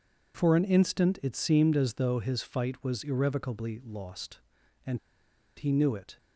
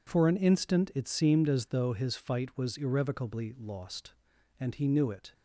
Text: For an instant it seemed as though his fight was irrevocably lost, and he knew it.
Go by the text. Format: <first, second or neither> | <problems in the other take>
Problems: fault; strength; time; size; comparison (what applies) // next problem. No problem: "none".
second | pauses between "and" and "he"; noticeable; at 4.9 s; 0.58 s long